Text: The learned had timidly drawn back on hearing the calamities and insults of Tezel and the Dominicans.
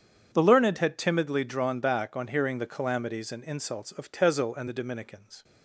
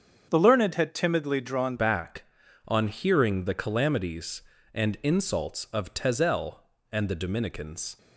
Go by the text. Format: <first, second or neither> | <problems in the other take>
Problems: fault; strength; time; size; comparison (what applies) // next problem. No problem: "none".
first | starts louder than the rest; strong; until 1.3 s; 7 dB; strong in the first // changes voice at "back"; from 1.7 s on; 6.2 s long